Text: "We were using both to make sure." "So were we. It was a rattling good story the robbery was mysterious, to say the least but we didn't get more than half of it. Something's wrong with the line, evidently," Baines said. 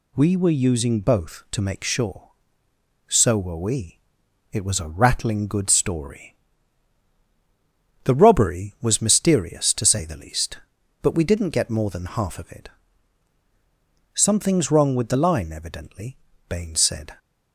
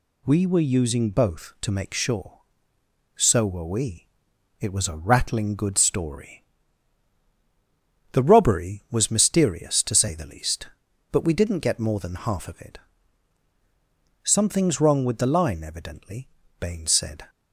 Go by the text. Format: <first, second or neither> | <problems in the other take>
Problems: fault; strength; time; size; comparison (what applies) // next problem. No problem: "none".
neither | pauses between "story" and "the"; strong; the same in both